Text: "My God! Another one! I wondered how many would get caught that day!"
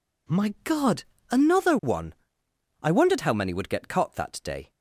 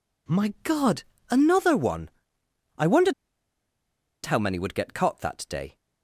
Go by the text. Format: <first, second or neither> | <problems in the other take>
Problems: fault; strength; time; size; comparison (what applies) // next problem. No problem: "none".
first | pauses between "wondered" and "how"; at 3.1 s; 1.1 s long